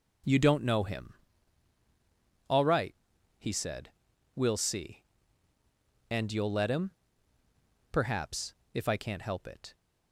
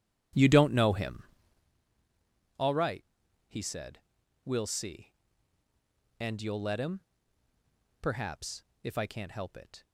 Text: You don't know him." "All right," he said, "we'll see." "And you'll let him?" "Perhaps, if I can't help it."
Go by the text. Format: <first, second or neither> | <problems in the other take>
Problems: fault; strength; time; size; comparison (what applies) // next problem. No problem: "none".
first | starts louder than the rest; strong; until 1.8 s; 10.5 dB